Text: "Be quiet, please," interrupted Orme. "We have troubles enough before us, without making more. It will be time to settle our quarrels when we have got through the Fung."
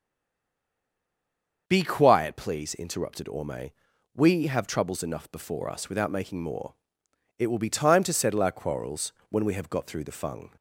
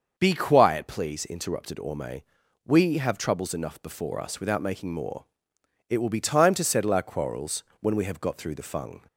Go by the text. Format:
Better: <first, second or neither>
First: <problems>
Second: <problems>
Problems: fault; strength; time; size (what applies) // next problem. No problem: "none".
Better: second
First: stays silent before the first word; noticeable; until 1.6 s; 1.6 s long // starts louder than the rest; until 2.6 s; 6.5 dB // pauses between "quarrels" and "when"; slight; at 9.1 s; 0.18 s long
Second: starts louder than the rest; until 1.1 s; 6.5 dB // pauses between "quarrels" and "when"; slight; at 7.6 s; 0.18 s long